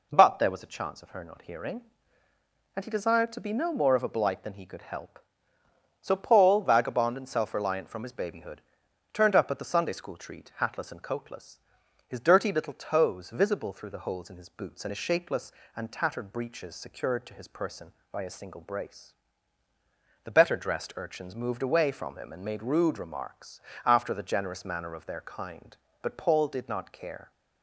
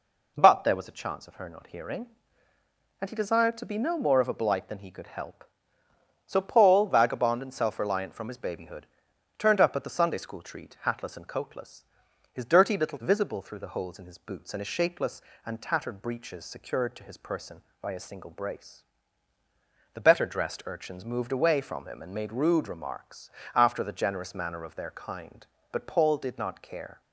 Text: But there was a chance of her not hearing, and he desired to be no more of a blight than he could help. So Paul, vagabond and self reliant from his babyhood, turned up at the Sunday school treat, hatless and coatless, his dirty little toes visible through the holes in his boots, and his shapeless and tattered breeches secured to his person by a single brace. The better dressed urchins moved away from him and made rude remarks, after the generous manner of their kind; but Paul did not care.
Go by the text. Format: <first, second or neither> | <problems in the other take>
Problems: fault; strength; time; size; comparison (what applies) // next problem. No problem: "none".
first | skips "toes"; at 12.9 s